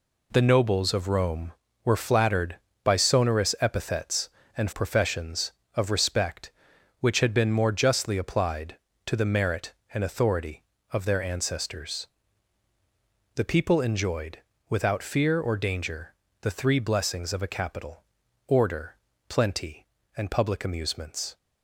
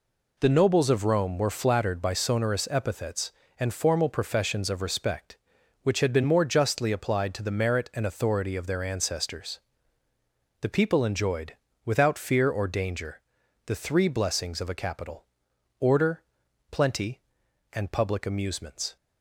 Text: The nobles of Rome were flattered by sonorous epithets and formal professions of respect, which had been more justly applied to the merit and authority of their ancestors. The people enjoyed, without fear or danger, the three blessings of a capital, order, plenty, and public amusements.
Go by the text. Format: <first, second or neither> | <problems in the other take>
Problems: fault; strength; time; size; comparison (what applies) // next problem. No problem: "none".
second | skips "formal"; at 4.7 s